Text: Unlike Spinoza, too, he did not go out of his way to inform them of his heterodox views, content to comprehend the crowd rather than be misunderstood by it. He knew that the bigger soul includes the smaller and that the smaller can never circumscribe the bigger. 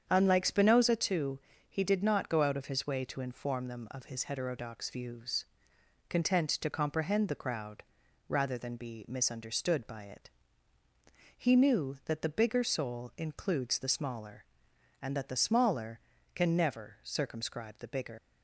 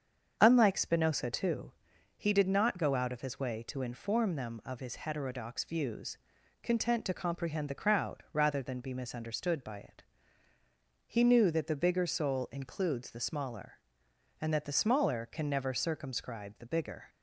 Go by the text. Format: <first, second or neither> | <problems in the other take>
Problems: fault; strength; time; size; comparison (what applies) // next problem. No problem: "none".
second | starts louder than the rest; strong; until 1.1 s; 8 dB; strong in the second // pauses between "crowd" and "rather"; noticeable; at 7.8 s; 0.46 s long // leaves "bigger" unfinished; at 18.1 s; 95 ms